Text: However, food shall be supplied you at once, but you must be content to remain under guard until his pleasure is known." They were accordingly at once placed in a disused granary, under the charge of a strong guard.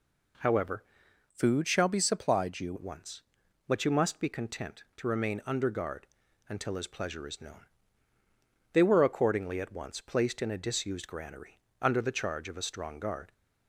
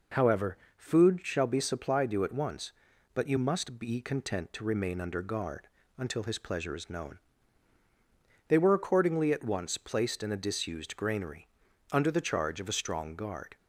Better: second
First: changes voice from "food" to "you"; from 1.2 to 2.7 s; 1.5 s long // pauses between "guard" and "until"; at 6.0 s; 0.42 s long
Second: pauses between "guard" and "until"; slight; at 5.6 s; 0.30 s long

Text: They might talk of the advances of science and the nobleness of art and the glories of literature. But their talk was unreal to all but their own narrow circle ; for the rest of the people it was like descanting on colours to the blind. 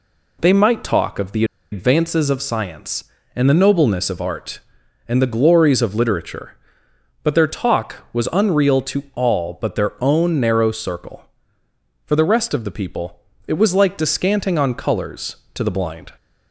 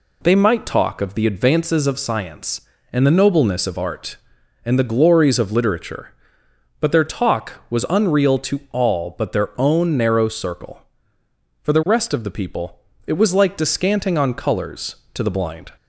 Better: second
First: pauses between "the" and "advances"; slight; at 1.4 s; 0.28 s long // pauses between "people" and "it"; slight; at 13.1 s; 0.28 s long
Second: pauses between "people" and "it"; slight; at 12.7 s; 0.28 s long

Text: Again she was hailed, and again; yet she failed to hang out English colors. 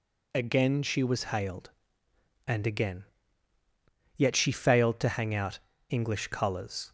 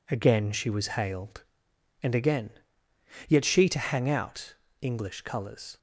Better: first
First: pauses between "out" and "English"; slight; at 5.5 s; 0.32 s long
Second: skips "failed"; at 3.6 s // pauses between "out" and "English"; slight; at 4.5 s; 0.28 s long

